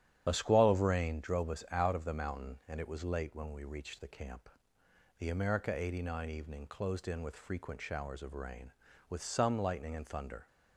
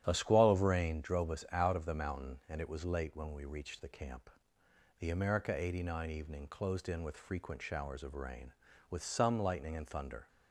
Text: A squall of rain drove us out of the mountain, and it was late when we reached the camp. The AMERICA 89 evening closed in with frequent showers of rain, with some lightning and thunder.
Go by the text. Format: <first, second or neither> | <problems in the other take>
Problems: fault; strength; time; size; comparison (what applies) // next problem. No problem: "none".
second | loses the start of "A"; at 0.2 s; 35 ms // starts louder than the rest; strong; until 1.2 s; 10 dB; strong in the second